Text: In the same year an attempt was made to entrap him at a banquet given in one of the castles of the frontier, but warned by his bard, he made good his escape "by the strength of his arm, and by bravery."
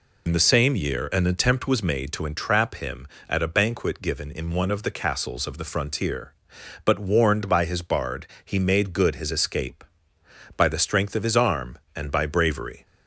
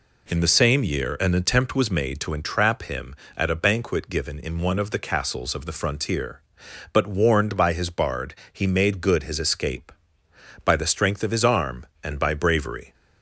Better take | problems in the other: second | loses the start of "In"; at 0.2 s; 70 ms

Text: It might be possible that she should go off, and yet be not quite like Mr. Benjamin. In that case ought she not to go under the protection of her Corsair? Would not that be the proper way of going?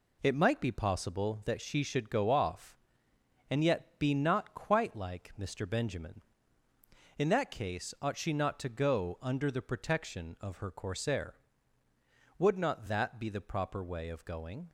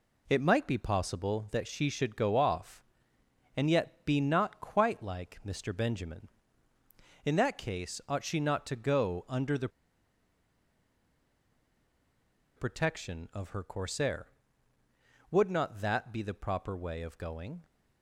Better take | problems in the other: first | pauses between "the" and "protection"; strong; at 9.6 s; 2.8 s long

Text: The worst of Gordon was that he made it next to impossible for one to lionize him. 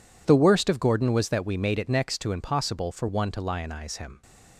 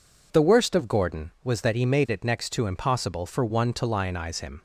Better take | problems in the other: second | says "we" for "he"; at 1.4 s

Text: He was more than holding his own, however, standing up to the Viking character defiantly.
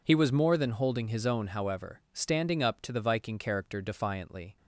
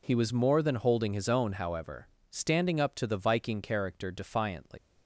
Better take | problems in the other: first | leaves "defiantly" unfinished; at 4.7 s; 180 ms

